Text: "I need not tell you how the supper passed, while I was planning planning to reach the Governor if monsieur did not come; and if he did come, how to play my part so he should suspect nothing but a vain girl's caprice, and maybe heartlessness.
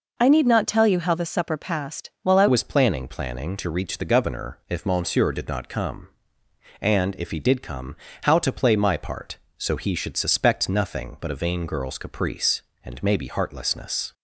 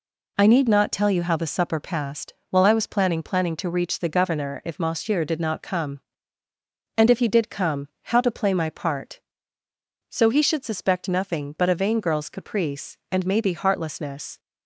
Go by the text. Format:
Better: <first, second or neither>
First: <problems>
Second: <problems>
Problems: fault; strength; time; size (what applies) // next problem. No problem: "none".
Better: second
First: changes voice at "was"; from 2.4 s on; 11.7 s long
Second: none